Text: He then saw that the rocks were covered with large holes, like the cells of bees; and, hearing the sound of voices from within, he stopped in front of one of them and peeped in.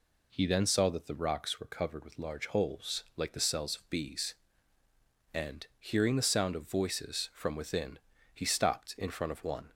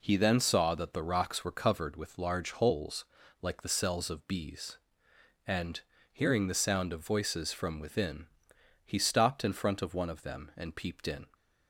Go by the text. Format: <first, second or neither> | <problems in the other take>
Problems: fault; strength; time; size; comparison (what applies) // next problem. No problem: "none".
second | stops before "of them and peeped in"; at 9.7 s